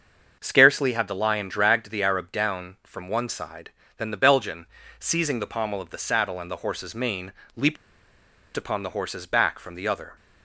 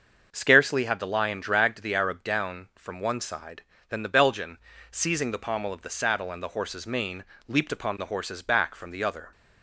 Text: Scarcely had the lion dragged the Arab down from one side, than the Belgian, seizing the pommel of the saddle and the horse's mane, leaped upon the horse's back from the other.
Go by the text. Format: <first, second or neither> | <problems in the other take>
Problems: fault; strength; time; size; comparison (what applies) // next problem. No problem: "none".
second | starts louder than the rest; until 1.4 s; 6.5 dB; also in the second // pauses between "leaped" and "upon"; noticeable; at 7.7 s; 0.80 s long